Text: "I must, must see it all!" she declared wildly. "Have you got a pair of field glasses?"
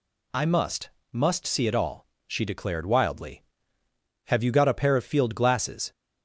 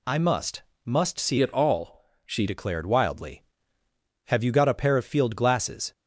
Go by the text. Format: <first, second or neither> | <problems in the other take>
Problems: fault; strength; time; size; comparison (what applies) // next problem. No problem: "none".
first | changes voice from "it" to "she"; from 1.3 to 2.4 s; 1.1 s long